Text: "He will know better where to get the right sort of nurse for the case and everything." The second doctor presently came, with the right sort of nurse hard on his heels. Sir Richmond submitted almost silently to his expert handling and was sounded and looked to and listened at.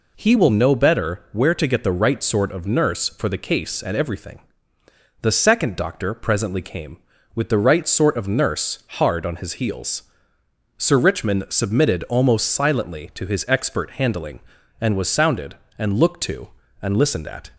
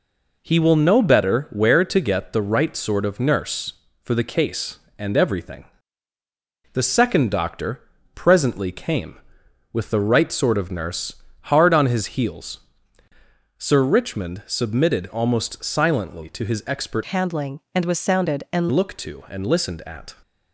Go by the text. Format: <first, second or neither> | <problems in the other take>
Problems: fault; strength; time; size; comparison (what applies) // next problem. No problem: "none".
first | pauses between "doctor" and "presently"; slight; at 7.8 s; 0.34 s long // pauses between "nurse" and "hard"; slight; at 11.1 s; 0.28 s long // changes voice from "handling" to "and"; from 17.0 to 18.6 s; 1.6 s long